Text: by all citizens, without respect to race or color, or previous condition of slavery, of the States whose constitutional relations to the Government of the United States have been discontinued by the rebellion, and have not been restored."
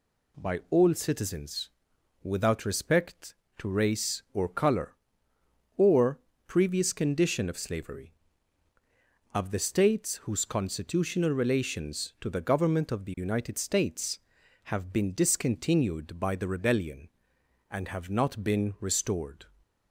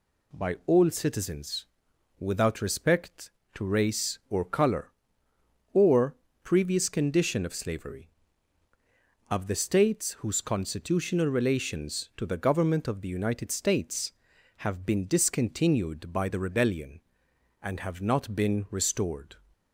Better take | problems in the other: neither | pauses between "or" and "previous"; slight; the same in both

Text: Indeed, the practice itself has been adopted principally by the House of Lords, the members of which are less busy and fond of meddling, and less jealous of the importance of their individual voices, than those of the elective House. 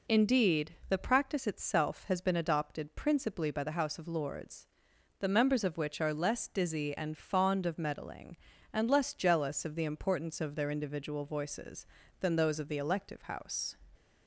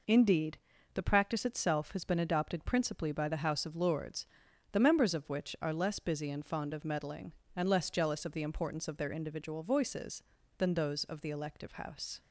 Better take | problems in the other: second | says "dizzy" for "busy"; at 6.4 s

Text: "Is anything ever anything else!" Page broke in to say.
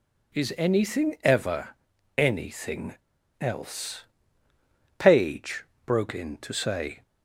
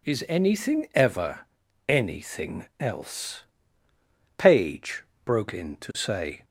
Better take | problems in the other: second | pauses between "ever" and "anything"; at 1.7 s; 0.42 s long; also in the second // pauses between "anything" and "else"; at 2.9 s; 0.43 s long // pauses between "Page" and "broke"; slight; at 5.6 s; 0.18 s long; slight in the second

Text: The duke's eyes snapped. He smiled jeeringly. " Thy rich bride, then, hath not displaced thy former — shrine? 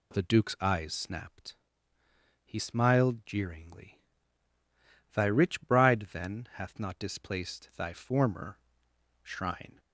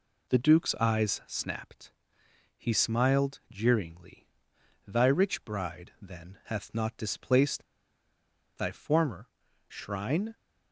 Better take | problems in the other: first | pauses between "displaced" and "thy"; noticeable; at 7.6 s; 0.93 s long

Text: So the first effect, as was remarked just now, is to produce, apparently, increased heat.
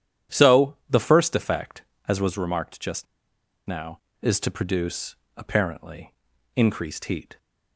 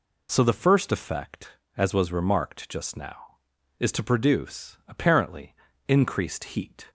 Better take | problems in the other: second | starts louder than the rest; strong; until 1.4 s; 10.5 dB // pauses between "just" and "now"; noticeable; at 3.0 s; 0.62 s long

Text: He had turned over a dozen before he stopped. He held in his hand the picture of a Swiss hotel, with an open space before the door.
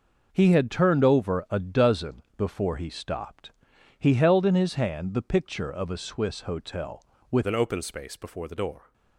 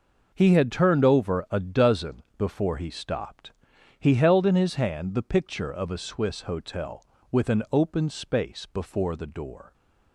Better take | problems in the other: second | changes voice at "an"; from 7.4 s on; 1.5 s long

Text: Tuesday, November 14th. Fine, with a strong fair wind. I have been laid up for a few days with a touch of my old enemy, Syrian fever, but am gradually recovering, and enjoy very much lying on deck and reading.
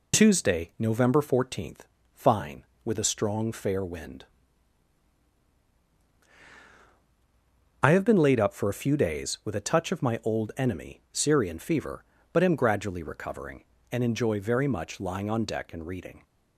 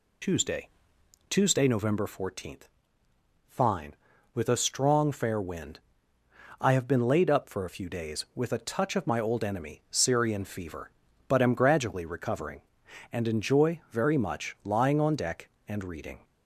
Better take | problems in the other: first | says "Tuesday" twice; at 1.2 s

